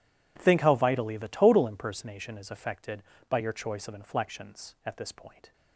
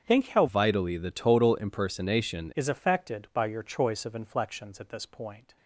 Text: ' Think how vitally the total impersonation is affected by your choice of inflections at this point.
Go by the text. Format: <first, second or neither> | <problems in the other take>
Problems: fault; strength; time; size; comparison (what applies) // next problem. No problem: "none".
first | starts louder than the rest; strong; until 1.0 s; 7.5 dB // changes voice from "vitally" to "impersonation"; from 0.4 to 2.5 s; 2.1 s long